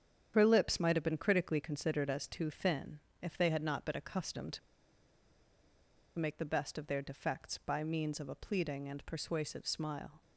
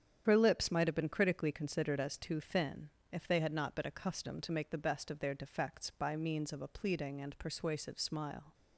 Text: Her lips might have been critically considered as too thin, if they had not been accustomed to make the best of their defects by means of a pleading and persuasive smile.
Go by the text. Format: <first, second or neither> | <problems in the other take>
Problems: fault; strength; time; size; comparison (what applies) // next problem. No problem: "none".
second | starts louder than the rest; strong; until 1.3 s; 8.5 dB; strong in the second // pauses between "to" and "make"; strong; at 4.5 s; 1.5 s long